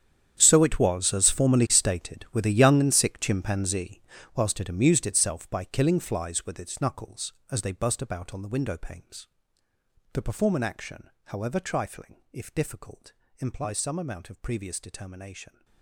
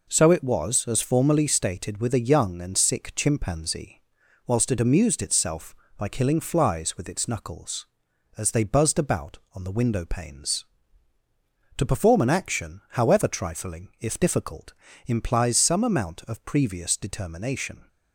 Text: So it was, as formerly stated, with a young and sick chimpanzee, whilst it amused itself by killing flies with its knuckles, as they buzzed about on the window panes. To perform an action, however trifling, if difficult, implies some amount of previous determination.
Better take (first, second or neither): second